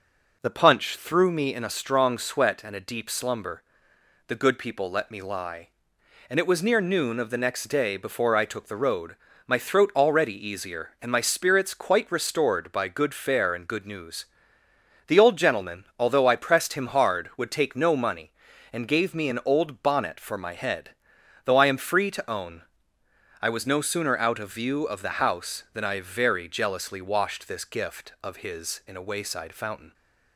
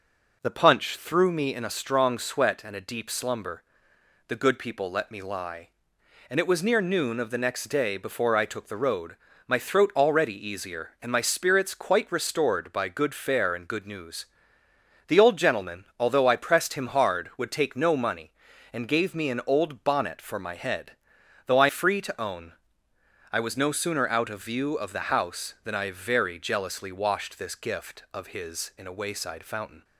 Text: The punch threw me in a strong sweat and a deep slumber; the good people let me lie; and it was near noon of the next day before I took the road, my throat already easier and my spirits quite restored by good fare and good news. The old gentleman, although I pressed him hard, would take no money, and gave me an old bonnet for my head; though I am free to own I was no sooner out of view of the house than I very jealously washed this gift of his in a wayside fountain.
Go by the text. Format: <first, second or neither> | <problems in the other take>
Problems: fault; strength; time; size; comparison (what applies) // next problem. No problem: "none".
first | skips "am"; at 21.6 s // pauses between "own" and "I"; noticeable; at 22.5 s; 0.80 s long; noticeable in the first